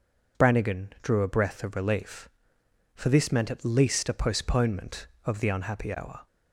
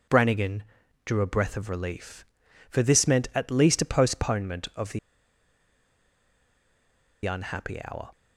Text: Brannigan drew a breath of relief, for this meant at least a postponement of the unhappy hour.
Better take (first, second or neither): first